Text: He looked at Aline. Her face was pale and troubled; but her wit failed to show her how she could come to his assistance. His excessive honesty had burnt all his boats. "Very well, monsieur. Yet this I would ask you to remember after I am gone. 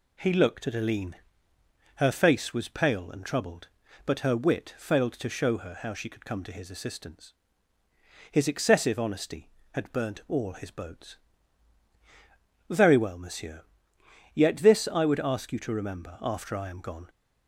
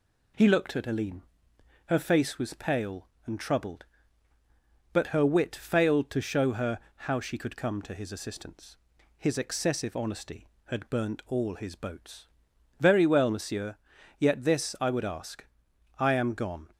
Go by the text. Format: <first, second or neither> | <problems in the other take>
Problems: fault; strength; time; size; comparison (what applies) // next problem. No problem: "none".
first | pauses between "her" and "how"; slight; at 6.7 s; 0.26 s long // skips "you to remember after"; at 15.7 s